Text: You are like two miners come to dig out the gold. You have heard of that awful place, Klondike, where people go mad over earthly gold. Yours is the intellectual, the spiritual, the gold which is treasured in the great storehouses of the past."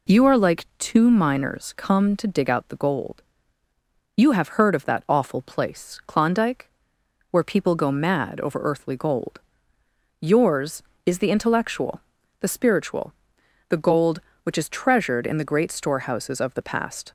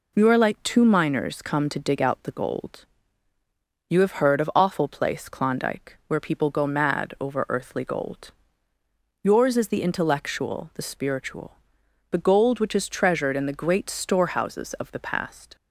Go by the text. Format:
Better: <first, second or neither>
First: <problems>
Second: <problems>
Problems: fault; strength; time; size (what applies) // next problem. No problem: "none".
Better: first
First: none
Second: skips "that"; at 4.5 s